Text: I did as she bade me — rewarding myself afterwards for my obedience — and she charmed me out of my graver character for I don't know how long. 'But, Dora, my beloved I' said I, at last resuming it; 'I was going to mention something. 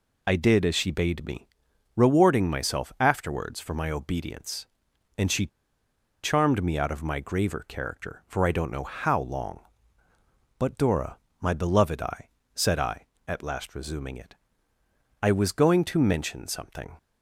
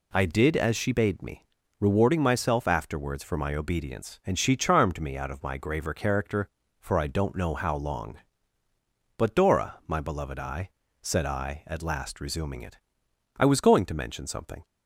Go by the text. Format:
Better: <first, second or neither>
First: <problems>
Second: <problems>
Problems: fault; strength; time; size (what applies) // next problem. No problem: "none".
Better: second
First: pauses between "she" and "charmed"; noticeable; at 5.4 s; 0.76 s long // pauses between "I" and "said"; slight; at 12.2 s; 0.26 s long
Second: pauses between "I" and "said"; slight; at 10.6 s; 0.30 s long